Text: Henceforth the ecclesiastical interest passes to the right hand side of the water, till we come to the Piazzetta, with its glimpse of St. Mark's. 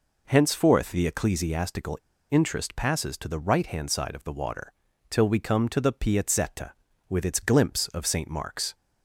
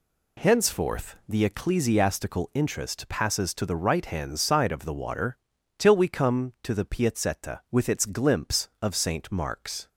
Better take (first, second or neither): second